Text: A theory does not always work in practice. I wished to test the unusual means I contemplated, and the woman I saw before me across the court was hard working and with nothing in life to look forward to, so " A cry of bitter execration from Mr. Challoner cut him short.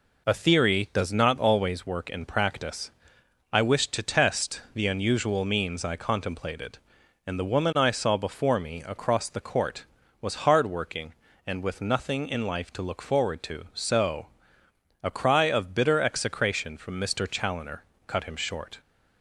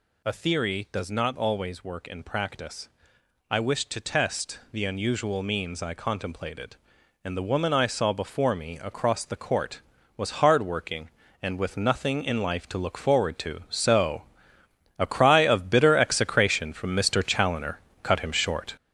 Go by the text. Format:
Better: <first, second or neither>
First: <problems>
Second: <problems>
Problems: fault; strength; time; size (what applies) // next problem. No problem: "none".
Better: first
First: pauses between "Challoner" and "cut"; slight; at 17.8 s; 0.24 s long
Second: gets louder; noticeable; throughout; 4 dB // pauses between "Challoner" and "cut"; slight; at 17.7 s; 0.24 s long